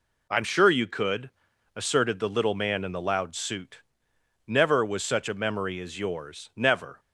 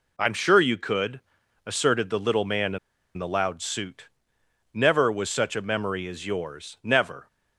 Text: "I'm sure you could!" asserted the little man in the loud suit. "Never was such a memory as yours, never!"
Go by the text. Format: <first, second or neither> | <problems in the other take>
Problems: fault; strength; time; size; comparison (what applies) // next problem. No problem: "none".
first | pauses between "in" and "the"; at 2.7 s; 0.38 s long